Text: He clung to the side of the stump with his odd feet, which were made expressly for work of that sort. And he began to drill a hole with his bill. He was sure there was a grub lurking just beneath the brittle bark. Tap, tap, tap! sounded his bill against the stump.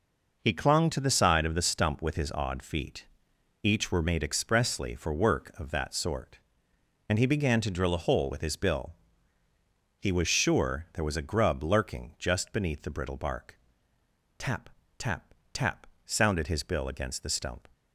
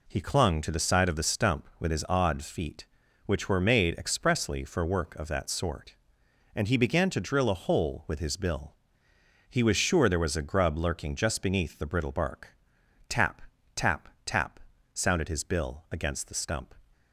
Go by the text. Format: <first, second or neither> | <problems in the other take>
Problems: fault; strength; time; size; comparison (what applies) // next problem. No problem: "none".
second | says "each" for "which"; at 3.6 s